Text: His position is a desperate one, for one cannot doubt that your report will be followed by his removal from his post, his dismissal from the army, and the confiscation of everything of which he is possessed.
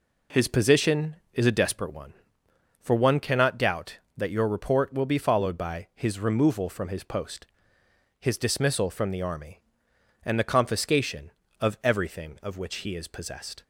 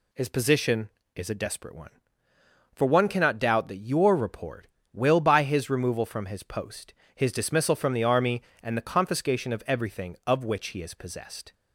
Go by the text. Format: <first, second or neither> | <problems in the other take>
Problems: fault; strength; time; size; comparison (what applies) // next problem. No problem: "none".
first | skips "be followed"; at 5.2 s